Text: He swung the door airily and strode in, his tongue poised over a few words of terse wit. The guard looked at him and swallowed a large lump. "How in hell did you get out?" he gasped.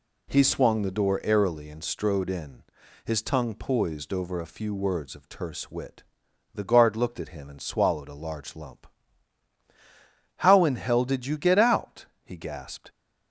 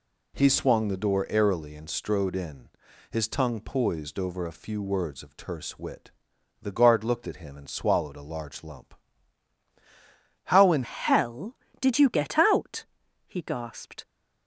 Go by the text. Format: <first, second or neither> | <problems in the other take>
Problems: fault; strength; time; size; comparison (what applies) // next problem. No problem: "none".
first | changes voice at "hell"; from 10.8 s on; 3.2 s long